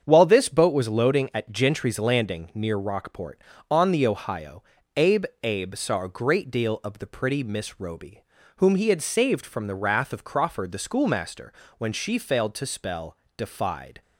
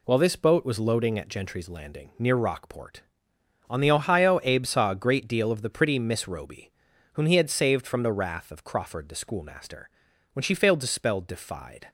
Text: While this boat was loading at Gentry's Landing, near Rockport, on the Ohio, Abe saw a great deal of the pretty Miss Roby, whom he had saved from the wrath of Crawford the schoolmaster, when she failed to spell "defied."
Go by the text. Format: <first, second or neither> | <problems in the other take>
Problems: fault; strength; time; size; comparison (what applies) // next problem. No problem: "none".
second | starts louder than the rest; strong; until 1.0 s; 7.5 dB // says "Abe" twice; at 5.4 s // pauses between "spell" and "defied"; slight; at 13.1 s; 0.22 s long